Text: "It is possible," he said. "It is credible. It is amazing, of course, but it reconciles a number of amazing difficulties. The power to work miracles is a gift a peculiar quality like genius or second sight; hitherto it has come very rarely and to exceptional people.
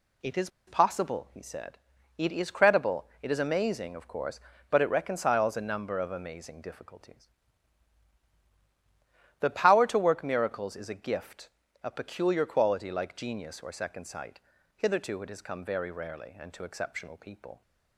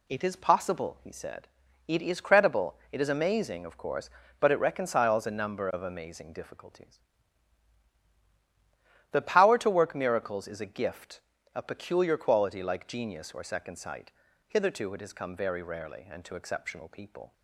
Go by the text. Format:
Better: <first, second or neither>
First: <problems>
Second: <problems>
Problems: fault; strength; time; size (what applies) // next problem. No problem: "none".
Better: second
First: pauses between "is" and "possible"; slight; at 0.4 s; 0.18 s long // pauses between "gift" and "a"; slight; at 11.4 s; 0.34 s long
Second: pauses between "gift" and "a"; slight; at 11.2 s; 0.34 s long